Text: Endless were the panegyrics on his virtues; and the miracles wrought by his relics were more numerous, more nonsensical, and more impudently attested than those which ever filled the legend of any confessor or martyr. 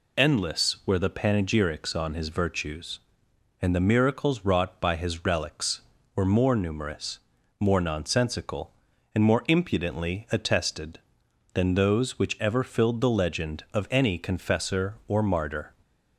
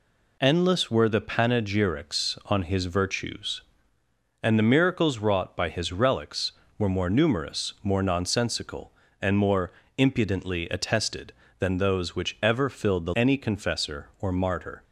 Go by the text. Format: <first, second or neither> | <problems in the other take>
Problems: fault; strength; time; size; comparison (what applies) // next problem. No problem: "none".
first | pauses between "more" and "impudently"; slight; at 9.7 s; 0.26 s long // skips "legend of"; at 13.1 s